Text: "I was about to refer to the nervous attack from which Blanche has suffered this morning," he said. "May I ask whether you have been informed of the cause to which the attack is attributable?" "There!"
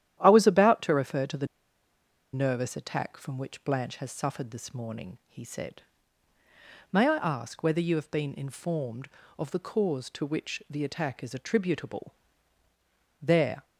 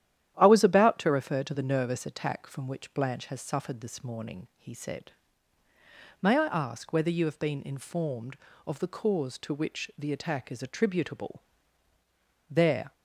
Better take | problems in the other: second | starts louder than the rest; strong; until 1.2 s; 11 dB; strong in the second // pauses between "the" and "nervous"; noticeable; at 1.4 s; 0.86 s long

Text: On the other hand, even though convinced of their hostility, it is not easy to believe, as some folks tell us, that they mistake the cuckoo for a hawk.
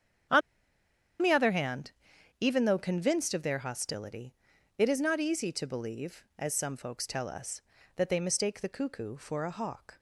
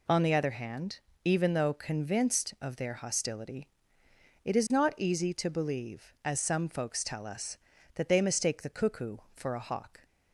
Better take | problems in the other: second | starts louder than the rest; strong; until 2.6 s; 8.5 dB // pauses between "On" and "the"; noticeable; at 0.4 s; 0.81 s long

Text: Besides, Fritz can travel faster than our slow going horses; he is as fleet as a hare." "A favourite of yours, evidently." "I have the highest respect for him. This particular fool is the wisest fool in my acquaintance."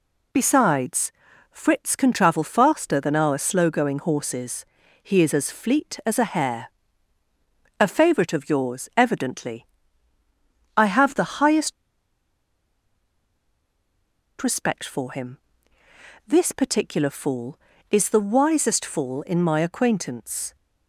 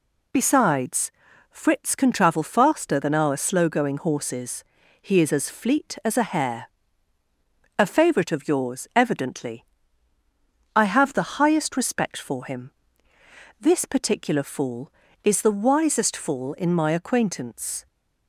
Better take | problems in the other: second | pauses between "highest" and "respect"; strong; at 11.7 s; 2.6 s long

